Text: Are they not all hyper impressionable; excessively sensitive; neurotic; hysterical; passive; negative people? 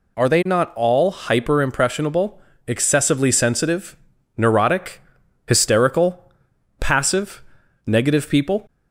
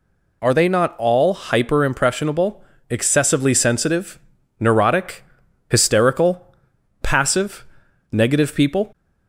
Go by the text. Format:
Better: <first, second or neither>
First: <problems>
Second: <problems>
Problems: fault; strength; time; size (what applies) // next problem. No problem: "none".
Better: neither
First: none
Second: none